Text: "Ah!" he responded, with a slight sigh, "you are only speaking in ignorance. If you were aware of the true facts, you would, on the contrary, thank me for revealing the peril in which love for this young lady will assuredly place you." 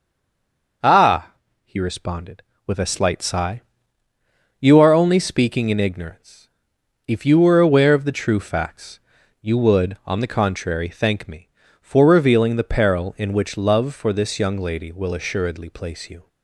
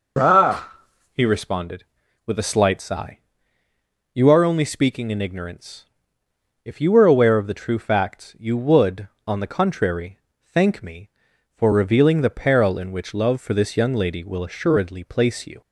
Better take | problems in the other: second | stays silent before the first word; slight; until 0.8 s; 0.8 s long

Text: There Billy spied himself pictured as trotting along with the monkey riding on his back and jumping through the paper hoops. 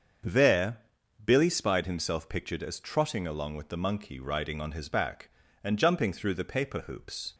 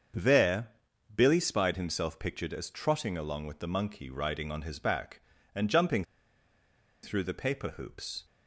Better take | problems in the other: first | starts louder than the rest; until 1.5 s; 7 dB; also in the first // pauses between "There" and "Billy"; at 0.6 s; 0.44 s long; also in the first // pauses between "jumping" and "through"; at 6.0 s; 0.98 s long

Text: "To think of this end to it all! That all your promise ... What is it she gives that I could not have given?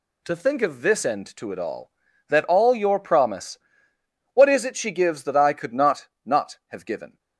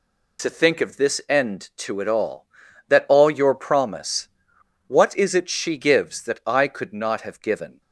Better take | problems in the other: second | says "not" twice; at 6.2 s

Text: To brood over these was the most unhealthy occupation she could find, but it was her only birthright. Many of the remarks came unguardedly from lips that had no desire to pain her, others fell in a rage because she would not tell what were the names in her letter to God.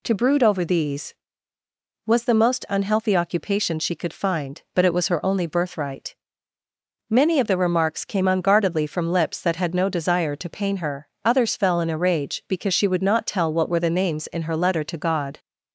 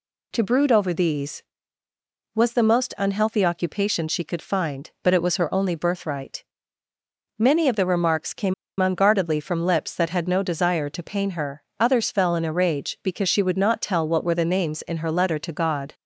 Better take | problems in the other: first | pauses between "came" and "unguardedly"; slight; at 8.5 s; 0.26 s long

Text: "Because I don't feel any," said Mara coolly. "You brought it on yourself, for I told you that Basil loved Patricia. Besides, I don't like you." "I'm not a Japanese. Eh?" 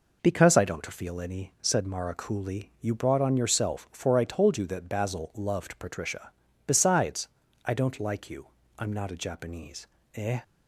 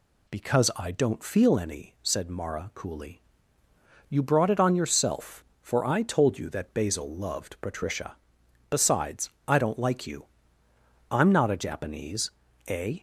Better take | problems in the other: second | skips "it"; at 3.2 s

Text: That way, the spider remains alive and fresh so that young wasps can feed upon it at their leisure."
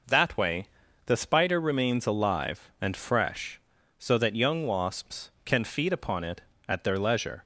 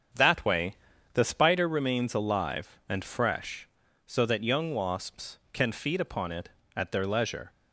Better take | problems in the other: first | starts louder than the rest; strong; until 1.8 s; 7.5 dB

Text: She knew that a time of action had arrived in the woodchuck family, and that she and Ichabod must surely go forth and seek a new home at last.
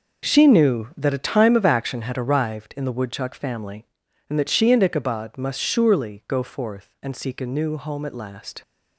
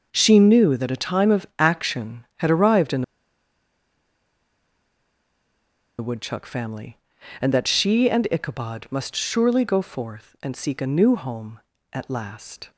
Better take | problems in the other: first | pauses between "in" and "the"; strong; at 3.0 s; 2.9 s long

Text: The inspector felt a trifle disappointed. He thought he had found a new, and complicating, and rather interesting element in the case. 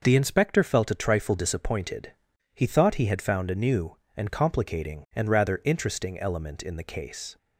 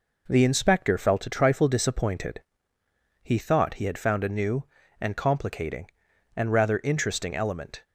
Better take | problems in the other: first | stops before "in the case"; at 7.8 s

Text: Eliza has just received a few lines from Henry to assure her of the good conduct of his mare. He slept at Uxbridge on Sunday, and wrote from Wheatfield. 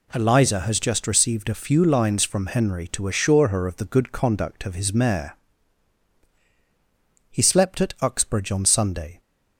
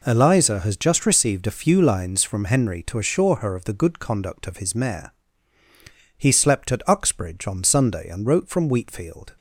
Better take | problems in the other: second | stops before "and wrote from Wheatfield"; at 9.1 s

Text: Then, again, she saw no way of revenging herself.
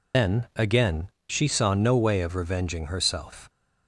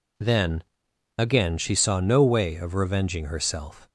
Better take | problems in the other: second | loses the start of "Then"; at 0.1 s; 95 ms

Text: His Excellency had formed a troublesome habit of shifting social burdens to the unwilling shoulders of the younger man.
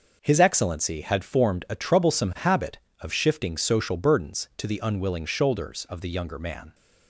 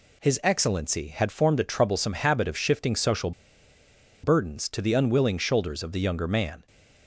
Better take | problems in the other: first | pauses between "social" and "burdens"; noticeable; at 3.3 s; 0.92 s long

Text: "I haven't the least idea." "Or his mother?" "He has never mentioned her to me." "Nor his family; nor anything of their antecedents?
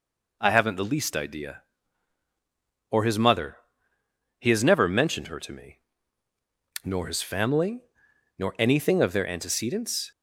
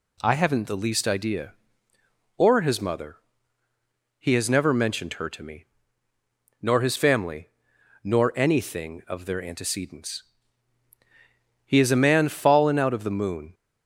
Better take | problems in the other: first | goes on to say "He is a man fallen out of the moon"; strong; from 11.6 s on; 1.8 s long

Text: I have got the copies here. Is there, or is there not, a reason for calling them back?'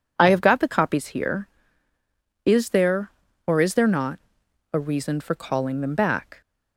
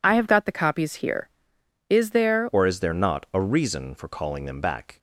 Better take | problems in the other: first | changes voice at "or"; from 2.5 s on; 2.4 s long

